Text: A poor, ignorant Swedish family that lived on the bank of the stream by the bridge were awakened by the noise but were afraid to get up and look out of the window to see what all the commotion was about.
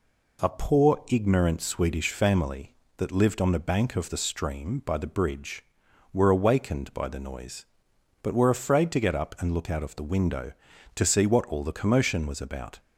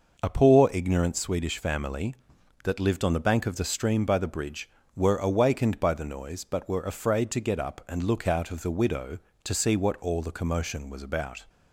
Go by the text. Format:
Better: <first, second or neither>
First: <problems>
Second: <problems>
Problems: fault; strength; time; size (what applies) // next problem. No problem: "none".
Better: first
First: none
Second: says "widow" for "window"; at 8.6 s